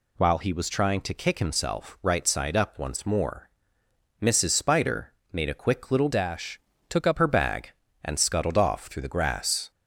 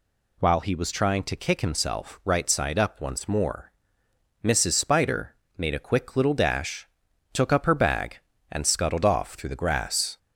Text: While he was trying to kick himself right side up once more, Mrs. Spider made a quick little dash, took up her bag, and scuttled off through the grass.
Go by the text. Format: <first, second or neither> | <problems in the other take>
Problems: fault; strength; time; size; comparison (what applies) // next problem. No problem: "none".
second | pauses between "Spider" and "made"; slight; at 5.1 s; 0.18 s long; slight in the second // changes voice from "dash" to "up"; from 6.1 to 7.1 s; 1.0 s long